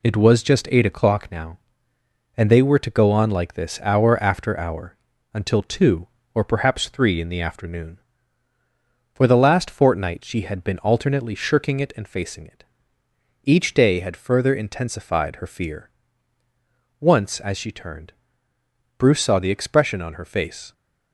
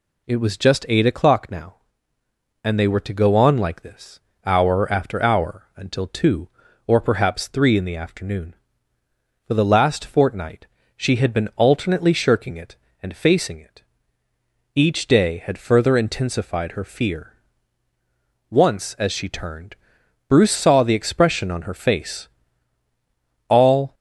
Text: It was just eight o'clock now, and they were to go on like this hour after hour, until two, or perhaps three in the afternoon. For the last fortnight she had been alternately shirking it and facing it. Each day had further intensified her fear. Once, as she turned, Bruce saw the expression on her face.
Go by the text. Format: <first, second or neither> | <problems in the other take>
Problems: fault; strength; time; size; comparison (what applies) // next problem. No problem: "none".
first | pauses between "this" and "hour"; slight; at 4.1 s; 0.24 s long // pauses between "fortnight" and "she"; slight; at 10.6 s; 0.30 s long // goes on to say "All"; slight; from 23.4 s on; 0.46 s long